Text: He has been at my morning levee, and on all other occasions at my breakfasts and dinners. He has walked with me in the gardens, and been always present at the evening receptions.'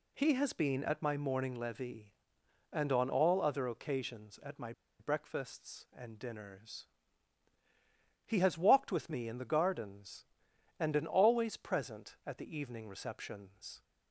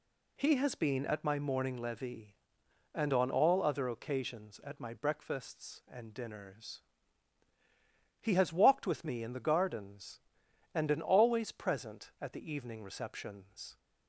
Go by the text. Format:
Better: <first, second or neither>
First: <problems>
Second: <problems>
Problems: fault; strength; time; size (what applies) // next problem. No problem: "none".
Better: second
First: pauses between "my" and "breakfasts"; slight; at 4.7 s; 0.28 s long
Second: none